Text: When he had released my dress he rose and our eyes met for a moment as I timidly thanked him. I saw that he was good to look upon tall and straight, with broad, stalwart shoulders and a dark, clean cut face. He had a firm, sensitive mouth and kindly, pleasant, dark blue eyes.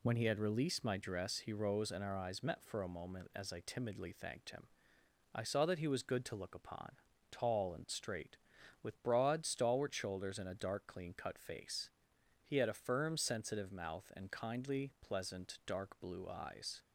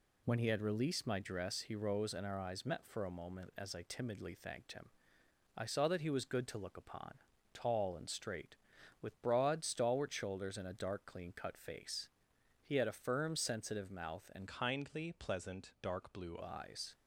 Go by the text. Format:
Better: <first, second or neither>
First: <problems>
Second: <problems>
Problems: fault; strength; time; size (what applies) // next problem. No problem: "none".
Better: first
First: pauses between "upon" and "tall"; at 6.9 s; 0.38 s long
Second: pauses between "upon" and "tall"; at 7.1 s; 0.38 s long // changes voice from "kindly" to "blue"; from 14.4 to 16.3 s; 1.9 s long